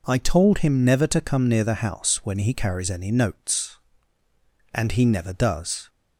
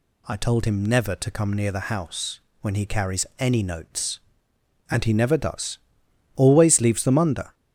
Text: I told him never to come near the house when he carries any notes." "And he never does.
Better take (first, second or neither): first